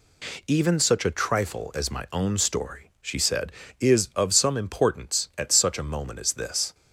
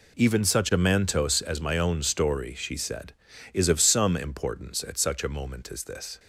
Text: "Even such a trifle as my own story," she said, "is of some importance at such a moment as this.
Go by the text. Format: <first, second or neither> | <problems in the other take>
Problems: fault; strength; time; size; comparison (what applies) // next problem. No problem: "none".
first | says "mantos" for "trifle"; at 0.7 s